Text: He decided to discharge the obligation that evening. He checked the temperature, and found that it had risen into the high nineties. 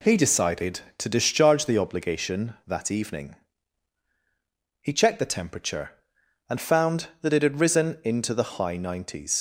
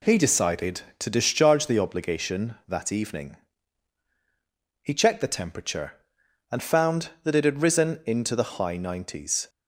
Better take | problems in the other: second | leaves "nineties" unfinished; at 9.3 s; 80 ms

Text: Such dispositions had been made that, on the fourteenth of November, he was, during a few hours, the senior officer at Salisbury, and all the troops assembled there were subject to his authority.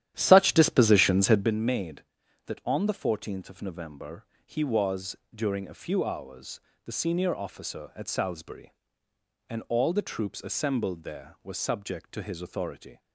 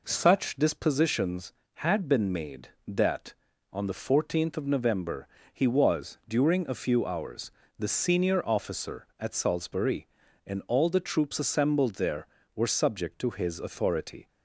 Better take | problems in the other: second | starts louder than the rest; strong; until 1.5 s; 11.5 dB

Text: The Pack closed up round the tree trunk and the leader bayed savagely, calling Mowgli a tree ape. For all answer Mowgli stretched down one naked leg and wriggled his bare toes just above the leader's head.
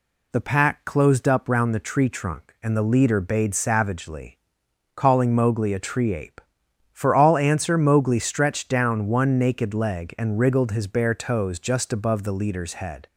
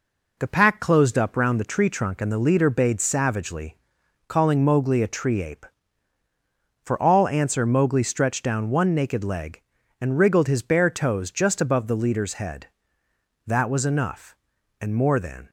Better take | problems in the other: first | goes on to say "That was enough and more than"; strong; from 13.4 s on; 2.0 s long

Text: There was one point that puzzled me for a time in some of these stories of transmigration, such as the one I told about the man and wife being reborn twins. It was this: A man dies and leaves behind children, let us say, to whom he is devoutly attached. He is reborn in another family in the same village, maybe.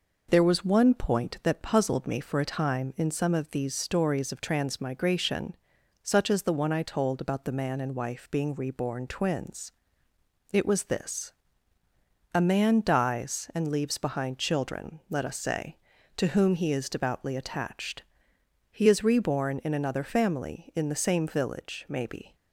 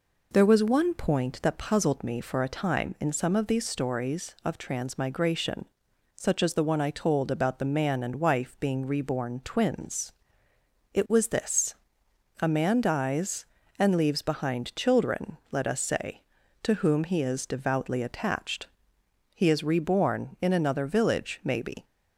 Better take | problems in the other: first | skips "family in the same"; at 20.8 s

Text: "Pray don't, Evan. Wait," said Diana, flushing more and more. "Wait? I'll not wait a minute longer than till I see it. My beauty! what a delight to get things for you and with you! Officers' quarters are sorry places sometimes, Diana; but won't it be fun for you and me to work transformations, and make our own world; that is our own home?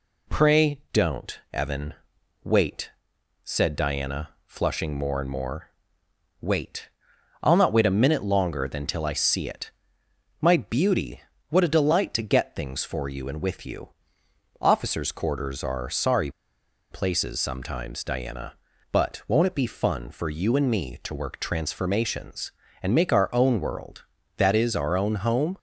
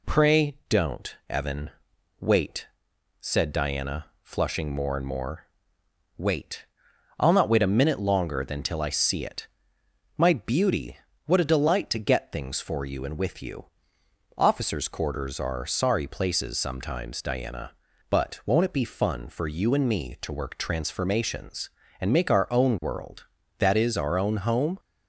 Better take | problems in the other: second | pauses between "sorry" and "places"; noticeable; at 16.3 s; 0.60 s long

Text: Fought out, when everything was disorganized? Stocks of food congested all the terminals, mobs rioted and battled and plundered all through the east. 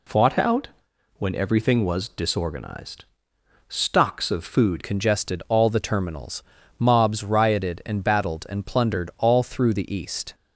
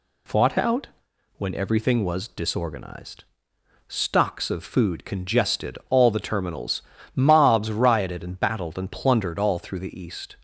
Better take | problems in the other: second | changes voice at "congested"; from 4.8 s on; 5.5 s long

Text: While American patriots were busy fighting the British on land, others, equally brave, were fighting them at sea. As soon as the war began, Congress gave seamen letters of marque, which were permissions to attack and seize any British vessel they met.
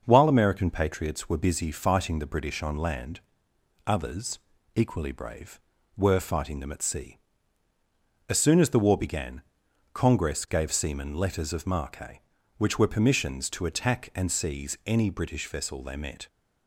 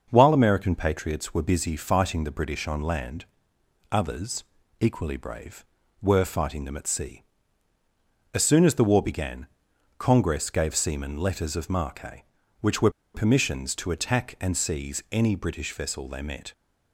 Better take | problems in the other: first | starts louder than the rest; until 1.1 s; 6.5 dB; also in the first // pauses between "were" and "permissions"; slight; at 12.8 s; 0.24 s long

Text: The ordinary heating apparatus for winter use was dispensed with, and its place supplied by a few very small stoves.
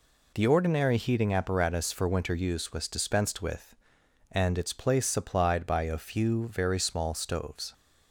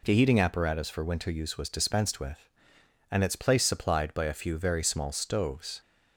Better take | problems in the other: first | skips "ordinary"; at 0.1 s

